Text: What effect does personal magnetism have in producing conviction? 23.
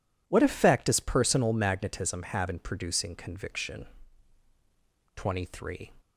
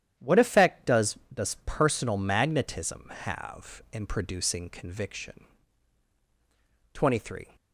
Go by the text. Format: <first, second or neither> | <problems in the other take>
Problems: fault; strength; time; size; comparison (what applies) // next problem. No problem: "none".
first | starts louder than the rest; strong; until 1.3 s; 10.5 dB // says "does" twice; at 1.3 s